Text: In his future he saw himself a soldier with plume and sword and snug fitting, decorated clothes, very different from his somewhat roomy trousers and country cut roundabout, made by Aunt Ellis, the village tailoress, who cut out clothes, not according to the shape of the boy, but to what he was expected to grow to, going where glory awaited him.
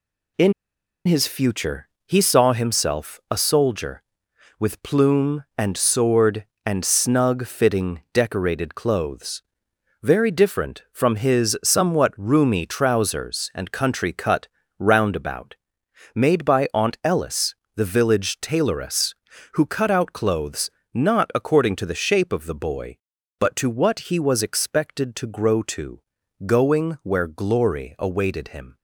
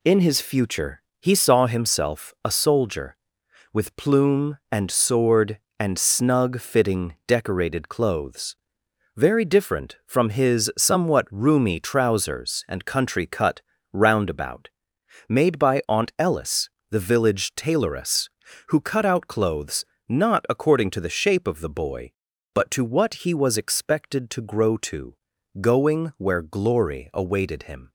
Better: second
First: pauses between "In" and "his"; noticeable; at 0.5 s; 0.54 s long // pauses between "future" and "he"; slight; at 1.8 s; 0.18 s long // pauses between "cut" and "roundabout"; slight; at 14.4 s; 0.32 s long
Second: pauses between "future" and "he"; slight; at 1.0 s; 0.18 s long // pauses between "cut" and "roundabout"; slight; at 13.6 s; 0.32 s long

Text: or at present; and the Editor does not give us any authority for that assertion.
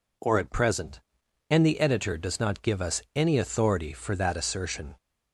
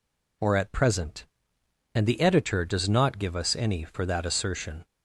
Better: first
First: none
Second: skips "authority"; at 3.8 s

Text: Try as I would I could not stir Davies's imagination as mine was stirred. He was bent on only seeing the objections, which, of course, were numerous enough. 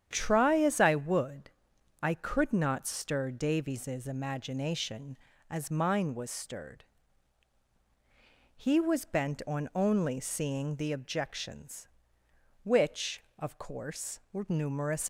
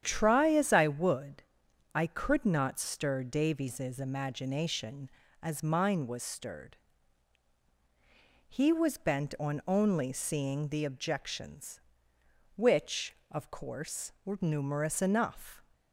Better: second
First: starts louder than the rest; strong; until 1.1 s; 9 dB // pauses between "would" and "I"; noticeable; at 1.5 s; 0.50 s long // stops before "enough"; at 15.0 s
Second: starts louder than the rest; strong; until 1.0 s; 9 dB // pauses between "would" and "I"; noticeable; at 1.4 s; 0.50 s long

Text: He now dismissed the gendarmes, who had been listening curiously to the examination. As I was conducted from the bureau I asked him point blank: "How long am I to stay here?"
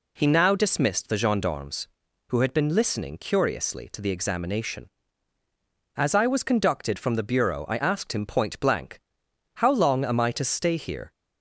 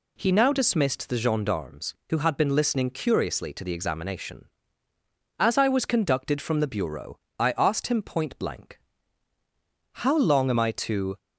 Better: first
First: none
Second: pauses between "bureau" and "I"; slight; at 7.1 s; 0.20 s long // stops before "stay here"; at 11.1 s

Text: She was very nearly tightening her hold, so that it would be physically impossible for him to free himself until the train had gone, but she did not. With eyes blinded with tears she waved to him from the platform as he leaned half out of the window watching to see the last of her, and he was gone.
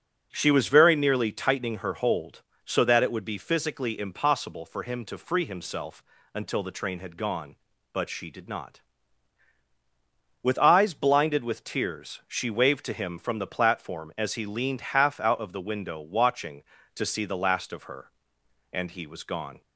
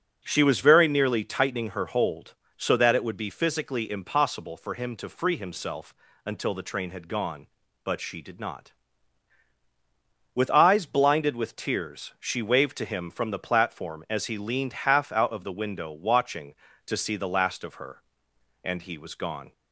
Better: neither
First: starts louder than the rest; noticeable; until 1.3 s; 6 dB // pauses between "himself" and "until"; slight; at 6.0 s; 0.32 s long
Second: starts louder than the rest; noticeable; until 1.2 s; 6 dB // pauses between "himself" and "until"; slight; at 5.9 s; 0.32 s long

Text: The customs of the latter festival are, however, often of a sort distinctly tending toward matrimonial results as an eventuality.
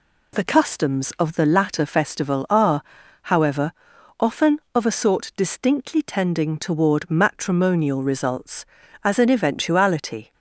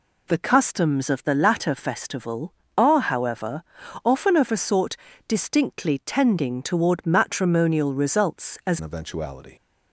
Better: first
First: none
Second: pauses between "sort" and "distinctly"; slight; at 4.9 s; 0.32 s long // changes voice at "an"; from 8.7 s on; 0.8 s long

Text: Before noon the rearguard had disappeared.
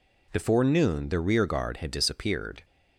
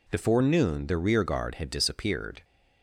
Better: neither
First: none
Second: none

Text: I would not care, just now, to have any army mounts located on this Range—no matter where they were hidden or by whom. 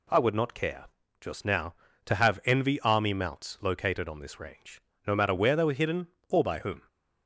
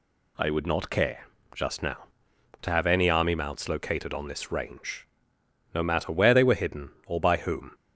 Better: second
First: says "envy" for "any"; at 2.4 s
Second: none

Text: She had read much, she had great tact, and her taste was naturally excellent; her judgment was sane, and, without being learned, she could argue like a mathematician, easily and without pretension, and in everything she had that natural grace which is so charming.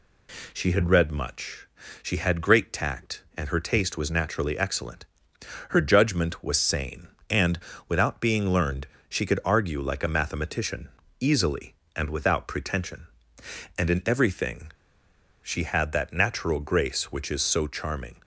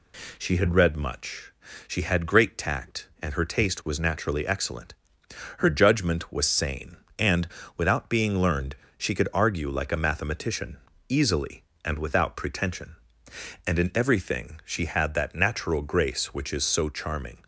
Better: second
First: pauses between "everything" and "she"; noticeable; at 14.6 s; 0.72 s long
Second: none

